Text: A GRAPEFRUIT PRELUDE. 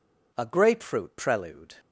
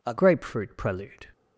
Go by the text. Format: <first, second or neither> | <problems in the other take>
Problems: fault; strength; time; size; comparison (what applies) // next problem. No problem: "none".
first | changes voice at "GRAPEFRUIT"; from 0.1 s on; 1.1 s long